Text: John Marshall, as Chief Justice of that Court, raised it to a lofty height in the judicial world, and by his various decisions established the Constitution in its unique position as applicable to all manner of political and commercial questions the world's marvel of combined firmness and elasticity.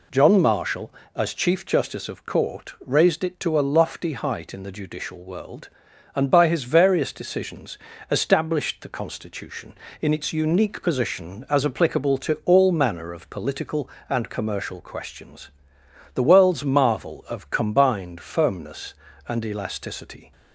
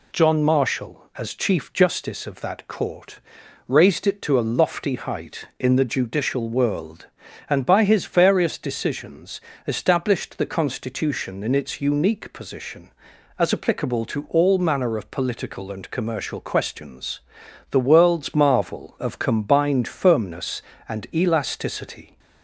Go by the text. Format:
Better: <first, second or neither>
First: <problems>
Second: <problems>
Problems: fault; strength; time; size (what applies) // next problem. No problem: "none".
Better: second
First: skips "that"; at 2.2 s // pauses between "decisions" and "established"; slight; at 7.7 s; 0.32 s long // pauses between "questions" and "the"; noticeable; at 15.4 s; 0.66 s long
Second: pauses between "decisions" and "established"; slight; at 9.4 s; 0.26 s long // pauses between "questions" and "the"; noticeable; at 17.2 s; 0.50 s long